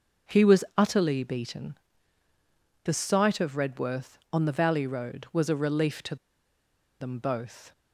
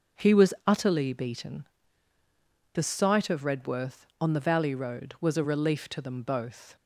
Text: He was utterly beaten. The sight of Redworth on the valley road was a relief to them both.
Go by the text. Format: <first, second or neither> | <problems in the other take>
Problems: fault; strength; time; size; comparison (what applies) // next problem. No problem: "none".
second | starts louder than the rest; until 1.4 s; 6.5 dB; also in the second // pauses between "to" and "them"; noticeable; at 6.1 s; 0.85 s long